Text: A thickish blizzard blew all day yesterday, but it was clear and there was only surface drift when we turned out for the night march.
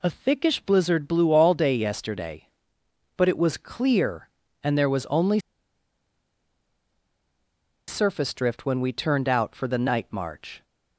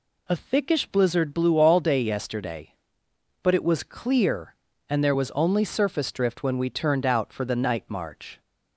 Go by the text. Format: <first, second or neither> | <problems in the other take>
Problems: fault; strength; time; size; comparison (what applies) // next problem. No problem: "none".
second | pauses between "only" and "surface"; strong; at 5.3 s; 2.4 s long